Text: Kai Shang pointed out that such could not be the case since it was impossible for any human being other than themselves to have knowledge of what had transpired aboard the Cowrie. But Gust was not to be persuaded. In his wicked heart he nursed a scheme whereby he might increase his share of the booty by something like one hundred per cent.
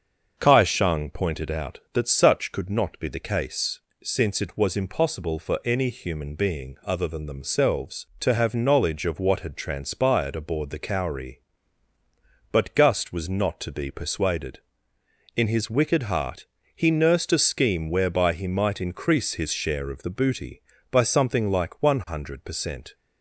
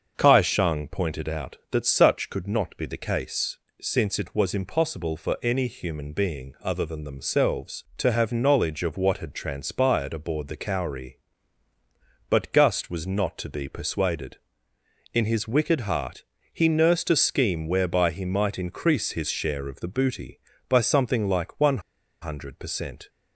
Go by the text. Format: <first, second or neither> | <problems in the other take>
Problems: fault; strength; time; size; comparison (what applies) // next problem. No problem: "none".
first | starts louder than the rest; until 1.1 s; 6.5 dB; also in the first // pauses between "case" and "since"; slight; at 3.5 s; 0.24 s long; slight in the first // pauses between "heart" and "he"; slight; at 16.2 s; 0.28 s long; slight in the first // pauses between "one" and "hundred"; at 21.7 s; 0.42 s long